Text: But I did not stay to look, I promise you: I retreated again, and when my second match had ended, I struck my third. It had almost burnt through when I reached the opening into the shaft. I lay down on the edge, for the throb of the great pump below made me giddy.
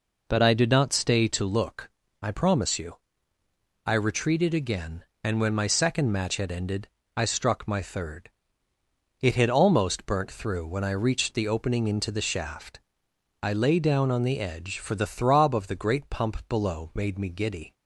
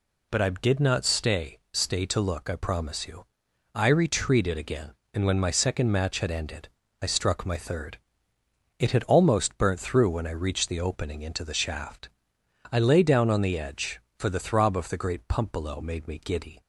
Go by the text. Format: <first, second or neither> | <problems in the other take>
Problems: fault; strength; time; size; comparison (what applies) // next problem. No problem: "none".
first | says "stay" twice; at 1.7 s